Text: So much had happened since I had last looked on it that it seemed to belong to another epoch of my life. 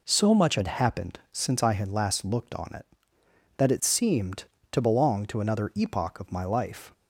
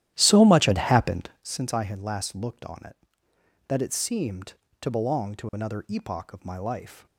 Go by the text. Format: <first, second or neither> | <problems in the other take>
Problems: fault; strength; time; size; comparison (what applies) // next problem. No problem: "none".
first | starts louder than the rest; strong; until 1.5 s; 13 dB